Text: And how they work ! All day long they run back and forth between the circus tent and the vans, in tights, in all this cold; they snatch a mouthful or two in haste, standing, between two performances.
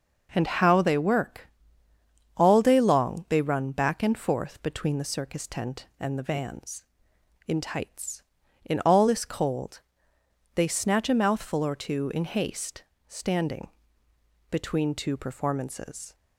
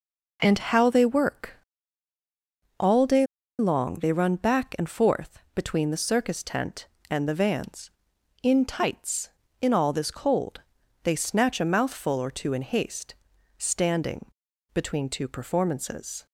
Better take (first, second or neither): first